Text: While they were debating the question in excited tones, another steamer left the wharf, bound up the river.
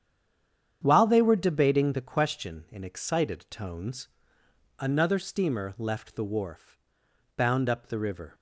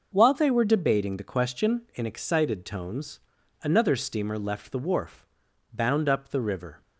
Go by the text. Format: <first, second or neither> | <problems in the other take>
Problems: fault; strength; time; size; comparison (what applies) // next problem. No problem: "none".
second | stays silent before the first word; slight; until 0.8 s; 0.8 s long // starts louder than the rest; strong; until 1.8 s; 8.5 dB